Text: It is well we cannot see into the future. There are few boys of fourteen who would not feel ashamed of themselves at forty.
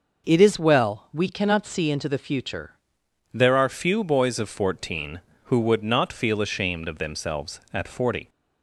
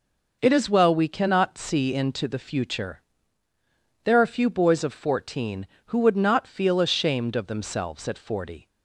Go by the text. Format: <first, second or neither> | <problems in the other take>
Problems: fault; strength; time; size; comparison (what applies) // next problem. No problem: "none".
second | changes voice at "There"; from 3.3 s on; 4.9 s long